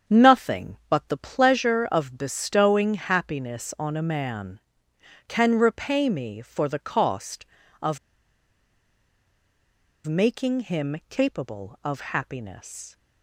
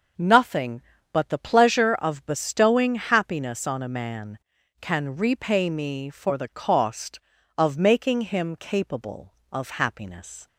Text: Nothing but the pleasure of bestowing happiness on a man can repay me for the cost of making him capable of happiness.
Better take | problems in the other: second | starts louder than the rest; strong; until 1.2 s; 8 dB // pauses between "of" and "making"; strong; at 7.9 s; 2.0 s long

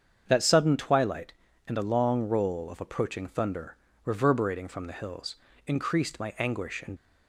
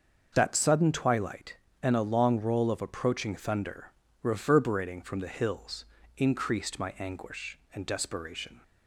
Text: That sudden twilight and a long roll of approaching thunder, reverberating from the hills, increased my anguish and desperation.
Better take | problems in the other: second | starts louder than the rest; strong; until 1.2 s; 7.5 dB; also in the second // stops before "desperation"; at 6.9 s

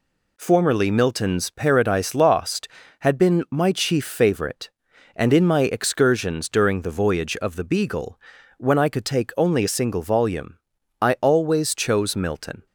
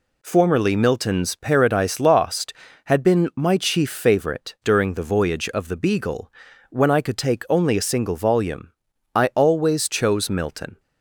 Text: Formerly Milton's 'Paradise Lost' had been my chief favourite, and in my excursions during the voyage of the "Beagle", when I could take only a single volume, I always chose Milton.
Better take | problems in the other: first | skips "and in my excursions"; at 4.5 s

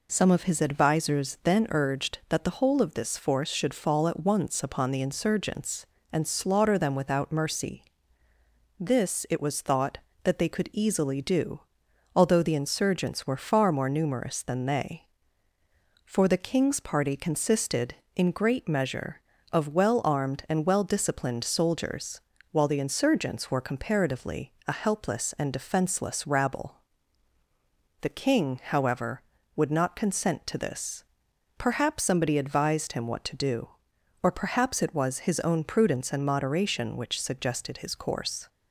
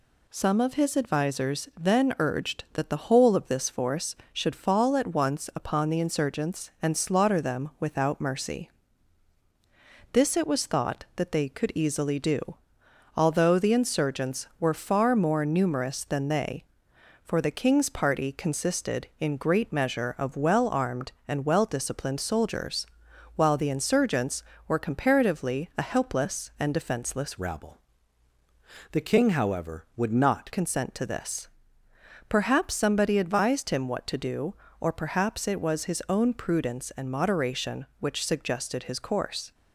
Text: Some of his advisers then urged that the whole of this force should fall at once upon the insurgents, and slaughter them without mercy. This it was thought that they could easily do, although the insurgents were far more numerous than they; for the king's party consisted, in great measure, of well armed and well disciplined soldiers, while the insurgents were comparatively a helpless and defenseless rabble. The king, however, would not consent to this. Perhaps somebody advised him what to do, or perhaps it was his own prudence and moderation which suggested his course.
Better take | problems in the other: first | changes voice from "rabble" to "not"; from 27.3 to 30.5 s; 3.2 s long

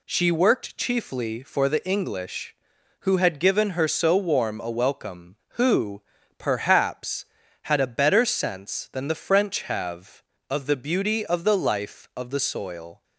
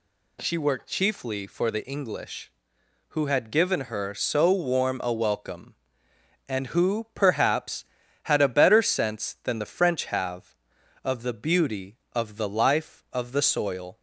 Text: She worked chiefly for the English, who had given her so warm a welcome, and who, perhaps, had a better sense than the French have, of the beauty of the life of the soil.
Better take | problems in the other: second | skips "and"; at 5.4 s

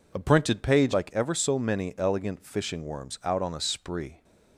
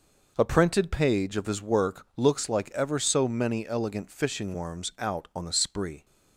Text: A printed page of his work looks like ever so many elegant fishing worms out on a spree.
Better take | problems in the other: second | skips "of his work looks"; at 0.9 s

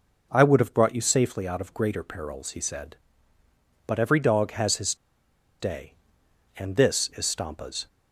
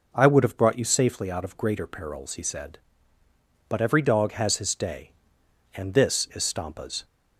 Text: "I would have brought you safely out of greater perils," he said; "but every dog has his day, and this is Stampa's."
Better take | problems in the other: second | pauses between "his" and "day"; noticeable; at 4.9 s; 0.65 s long

